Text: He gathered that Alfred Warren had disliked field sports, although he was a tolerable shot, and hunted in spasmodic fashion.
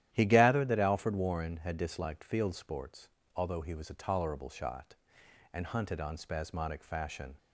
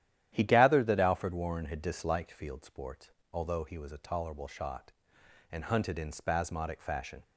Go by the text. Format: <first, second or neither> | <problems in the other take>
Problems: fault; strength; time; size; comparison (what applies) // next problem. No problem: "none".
second | starts louder than the rest; strong; until 1.1 s; 11.5 dB; strong in the second // says "on" for "in"; at 6.0 s